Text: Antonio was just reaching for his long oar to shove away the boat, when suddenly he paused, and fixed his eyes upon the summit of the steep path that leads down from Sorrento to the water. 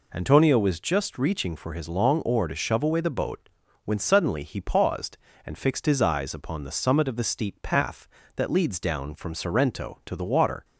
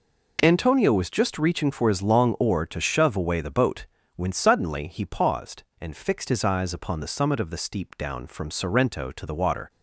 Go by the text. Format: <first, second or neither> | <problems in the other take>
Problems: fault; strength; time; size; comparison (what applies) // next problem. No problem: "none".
first | skips "path that leads"; at 7.9 s